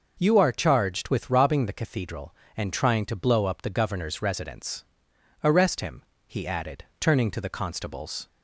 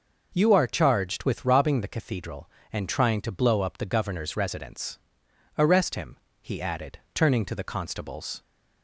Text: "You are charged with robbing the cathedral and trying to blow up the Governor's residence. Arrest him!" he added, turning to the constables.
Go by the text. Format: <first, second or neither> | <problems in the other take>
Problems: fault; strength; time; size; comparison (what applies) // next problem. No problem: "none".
neither | none